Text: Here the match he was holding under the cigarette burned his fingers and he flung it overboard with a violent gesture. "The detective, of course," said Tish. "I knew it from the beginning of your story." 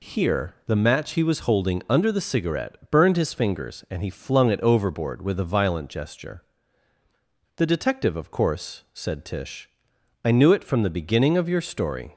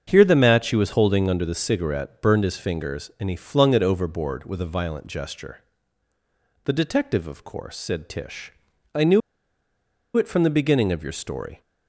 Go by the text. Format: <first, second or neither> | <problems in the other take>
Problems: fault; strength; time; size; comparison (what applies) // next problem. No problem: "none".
first | starts louder than the rest; strong; until 1.0 s; 7.5 dB // pauses between "knew" and "it"; noticeable; at 9.2 s; 0.96 s long